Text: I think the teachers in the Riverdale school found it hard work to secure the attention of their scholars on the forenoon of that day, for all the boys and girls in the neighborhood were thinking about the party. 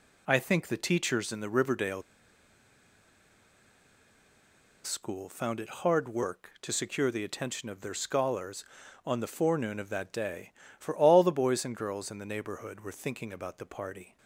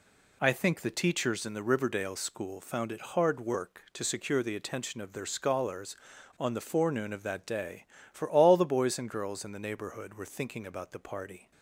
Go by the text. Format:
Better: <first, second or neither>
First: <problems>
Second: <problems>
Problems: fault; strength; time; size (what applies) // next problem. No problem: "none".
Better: second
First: pauses between "Riverdale" and "school"; strong; at 2.0 s; 2.8 s long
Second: none